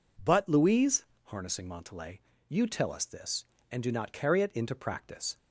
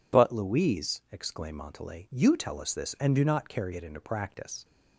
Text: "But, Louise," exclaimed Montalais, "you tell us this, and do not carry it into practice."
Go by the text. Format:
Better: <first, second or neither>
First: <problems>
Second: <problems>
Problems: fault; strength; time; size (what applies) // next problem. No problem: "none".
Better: second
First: says "harnessing" for "exclaimed"; at 1.2 s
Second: none